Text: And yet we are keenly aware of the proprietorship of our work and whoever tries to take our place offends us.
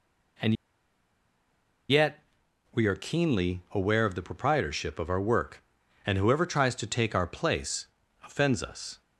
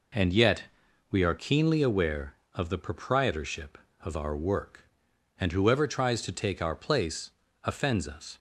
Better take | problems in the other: second | pauses between "And" and "yet"; strong; at 0.5 s; 1.3 s long // pauses between "yet" and "we"; noticeable; at 2.2 s; 0.50 s long; noticeable in the second // pauses between "place" and "offends"; slight; at 7.8 s; 0.36 s long; slight in the second

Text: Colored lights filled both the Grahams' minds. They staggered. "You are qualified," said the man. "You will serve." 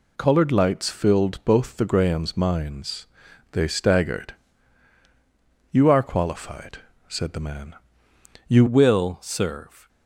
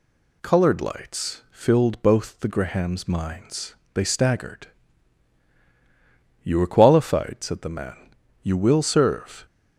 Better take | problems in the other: second | changes voice at "will"; from 8.6 s on; 1.2 s long

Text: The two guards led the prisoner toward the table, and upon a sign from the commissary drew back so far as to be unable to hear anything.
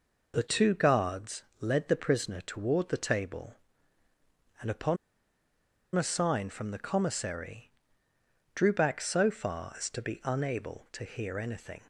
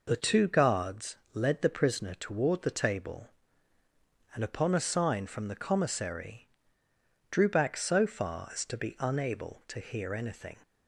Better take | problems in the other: second | pauses between "guards" and "led"; slight; at 1.4 s; 0.18 s long; slight in the second // pauses between "upon" and "a"; at 4.9 s; 0.98 s long // pauses between "commissary" and "drew"; noticeable; at 7.7 s; 0.82 s long; noticeable in the second

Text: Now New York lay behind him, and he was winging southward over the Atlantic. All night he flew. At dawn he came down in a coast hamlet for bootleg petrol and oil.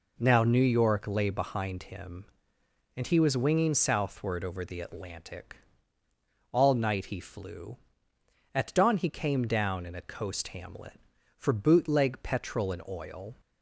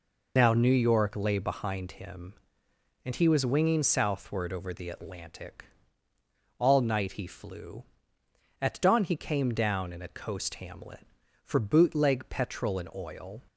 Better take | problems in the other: first | loses the start of "Now"; at 0.3 s; 75 ms

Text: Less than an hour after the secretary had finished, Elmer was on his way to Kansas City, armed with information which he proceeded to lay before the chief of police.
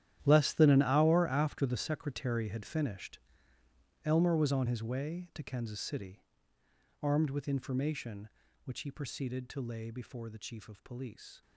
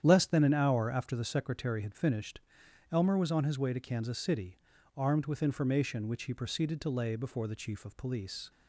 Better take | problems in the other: second | gets quieter; strong; throughout; 15.5 dB // starts louder than the rest; strong; until 1.2 s; 11.5 dB; strong in the second

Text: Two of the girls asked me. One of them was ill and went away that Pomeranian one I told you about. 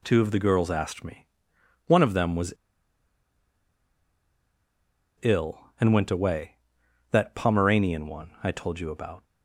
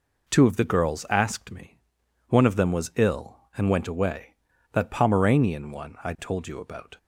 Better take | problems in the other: second | pauses between "was" and "ill"; strong; at 2.5 s; 2.6 s long

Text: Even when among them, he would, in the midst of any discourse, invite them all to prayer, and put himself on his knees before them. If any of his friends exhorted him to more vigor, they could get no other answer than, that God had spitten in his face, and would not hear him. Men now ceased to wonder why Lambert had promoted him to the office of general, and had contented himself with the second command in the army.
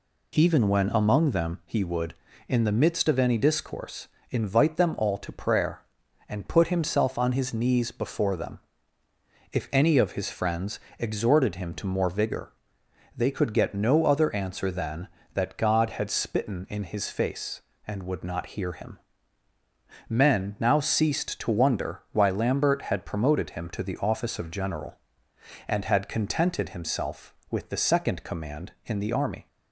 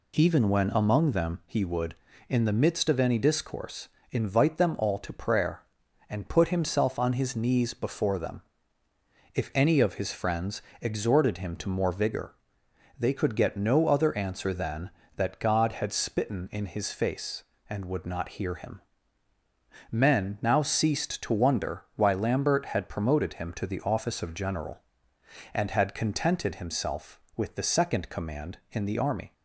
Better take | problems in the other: neither | pauses between "friends" and "exhorted"; slight; the same in both

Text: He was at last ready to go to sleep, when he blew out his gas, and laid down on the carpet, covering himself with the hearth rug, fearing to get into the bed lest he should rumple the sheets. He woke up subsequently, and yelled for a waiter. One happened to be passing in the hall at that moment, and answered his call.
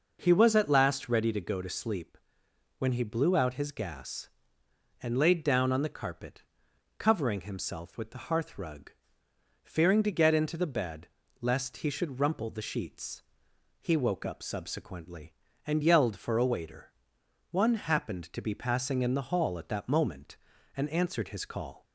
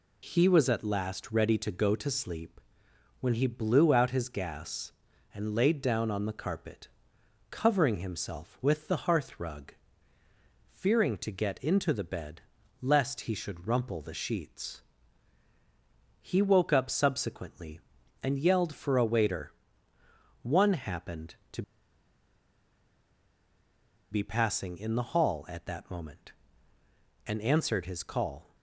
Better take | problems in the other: first | pauses between "bed" and "lest"; at 12.3 s; 0.40 s long; slight in the first // pauses between "to" and "be"; strong; at 21.6 s; 2.4 s long

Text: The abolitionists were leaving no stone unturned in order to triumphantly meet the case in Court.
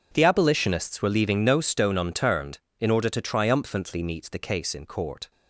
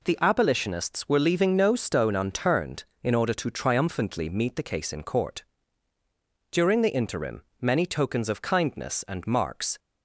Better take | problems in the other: first | goes on to say "During the interim many tokens of kindness and marks"; strong; from 6.5 s on; 3.2 s long

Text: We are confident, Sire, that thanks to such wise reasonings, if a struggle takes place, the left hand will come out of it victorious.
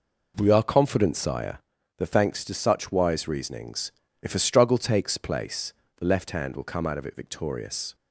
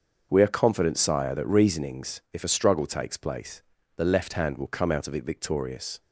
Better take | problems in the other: first | starts louder than the rest; until 1.3 s; 6.5 dB // skips "thanks to such wise"; at 1.4 s

